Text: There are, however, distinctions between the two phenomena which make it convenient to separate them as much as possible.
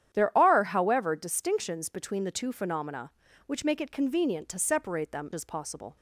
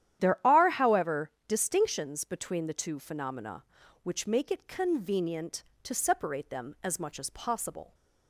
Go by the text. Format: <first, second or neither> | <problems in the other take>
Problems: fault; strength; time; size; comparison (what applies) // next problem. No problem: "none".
second | starts louder than the rest; strong; until 1.1 s; 10 dB; strong in the second // skips "as much"; at 5.3 s